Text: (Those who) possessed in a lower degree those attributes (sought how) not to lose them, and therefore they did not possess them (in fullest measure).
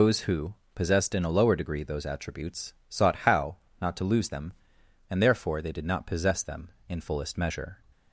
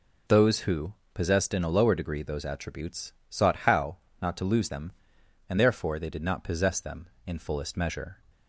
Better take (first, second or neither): second